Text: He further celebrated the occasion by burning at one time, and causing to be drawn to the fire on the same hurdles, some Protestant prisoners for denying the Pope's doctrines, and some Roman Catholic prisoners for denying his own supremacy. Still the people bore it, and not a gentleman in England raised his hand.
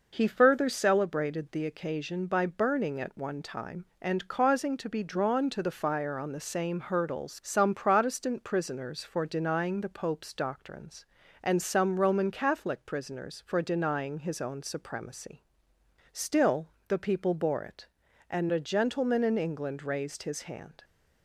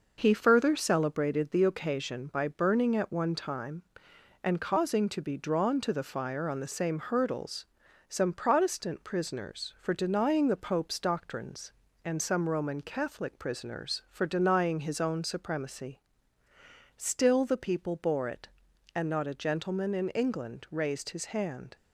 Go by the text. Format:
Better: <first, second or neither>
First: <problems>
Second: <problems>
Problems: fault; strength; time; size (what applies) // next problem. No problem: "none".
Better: second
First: pauses between "Still" and "the"; slight; at 16.6 s; 0.22 s long // skips "not"; at 18.4 s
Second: none